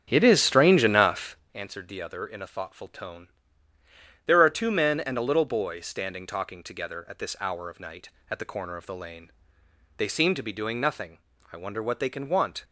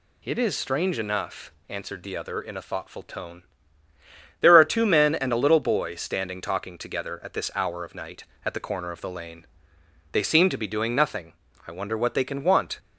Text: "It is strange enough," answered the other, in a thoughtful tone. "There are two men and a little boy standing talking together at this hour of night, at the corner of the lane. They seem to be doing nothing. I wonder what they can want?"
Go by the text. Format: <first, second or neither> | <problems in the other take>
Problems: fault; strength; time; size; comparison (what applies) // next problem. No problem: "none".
second | starts louder than the rest; strong; until 1.4 s; 8 dB